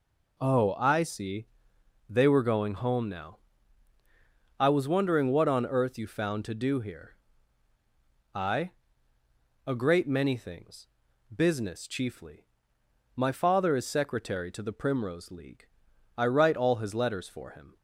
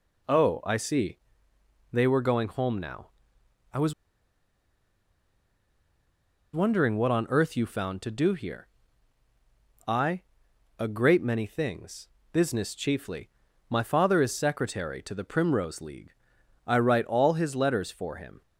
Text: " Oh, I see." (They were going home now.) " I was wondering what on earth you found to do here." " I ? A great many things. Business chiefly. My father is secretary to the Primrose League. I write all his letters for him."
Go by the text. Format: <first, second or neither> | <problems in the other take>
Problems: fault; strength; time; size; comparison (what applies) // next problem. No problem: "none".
first | pauses between "was" and "wondering"; strong; at 3.9 s; 2.5 s long